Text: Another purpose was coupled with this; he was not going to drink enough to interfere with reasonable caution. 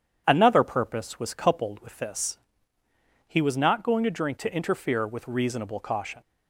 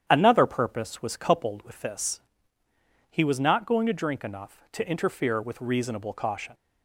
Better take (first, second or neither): second